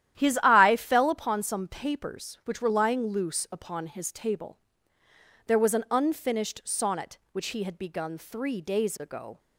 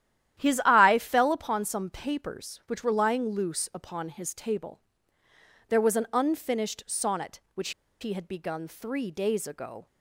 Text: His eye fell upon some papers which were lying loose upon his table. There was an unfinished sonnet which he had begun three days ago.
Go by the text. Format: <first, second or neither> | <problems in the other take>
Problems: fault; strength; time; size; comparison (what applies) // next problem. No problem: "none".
first | starts louder than the rest; strong; until 1.4 s; 11.5 dB; strong in the first // pauses between "which" and "he"; slight; at 7.7 s; 0.30 s long